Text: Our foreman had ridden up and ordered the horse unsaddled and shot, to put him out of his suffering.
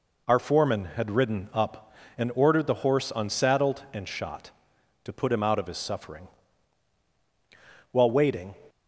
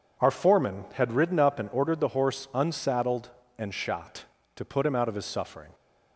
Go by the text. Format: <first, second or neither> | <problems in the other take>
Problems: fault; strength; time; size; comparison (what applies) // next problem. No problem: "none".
second | goes on to say "While waiting"; noticeable; from 7.9 s on; 0.64 s long